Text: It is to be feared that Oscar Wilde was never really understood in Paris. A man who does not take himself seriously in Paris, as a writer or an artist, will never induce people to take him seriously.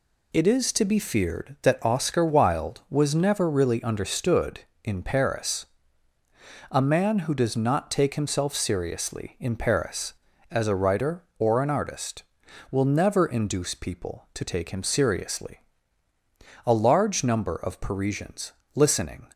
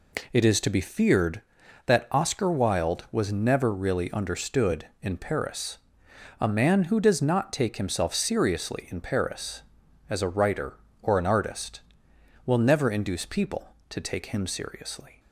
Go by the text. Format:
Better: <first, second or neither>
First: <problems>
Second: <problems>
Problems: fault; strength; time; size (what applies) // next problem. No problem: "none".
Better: second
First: goes on to say "A large number of Parisians listening"; strong; from 16.6 s on; 2.6 s long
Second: none